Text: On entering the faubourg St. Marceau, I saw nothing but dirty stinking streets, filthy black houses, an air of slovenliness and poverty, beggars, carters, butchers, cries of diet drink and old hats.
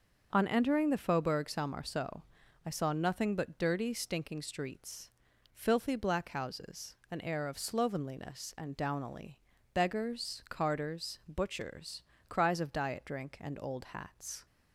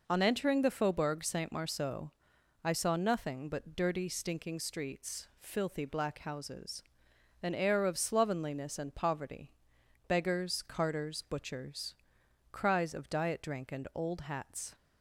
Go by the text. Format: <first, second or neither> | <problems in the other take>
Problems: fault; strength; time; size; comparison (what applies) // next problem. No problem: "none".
second | starts louder than the rest; until 1.3 s; 6.5 dB // says "downily" for "poverty"; at 8.7 s